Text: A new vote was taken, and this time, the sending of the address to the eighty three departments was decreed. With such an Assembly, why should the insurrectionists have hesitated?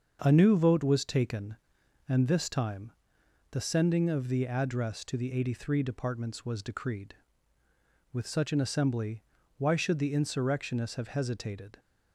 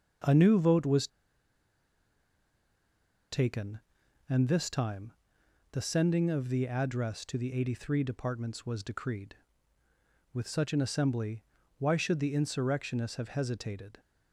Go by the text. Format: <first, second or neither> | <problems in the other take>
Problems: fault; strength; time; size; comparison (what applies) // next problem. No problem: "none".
first | starts louder than the rest; until 3.4 s; 6.5 dB; also in the first // pauses between "was" and "taken"; strong; at 1.0 s; 2.2 s long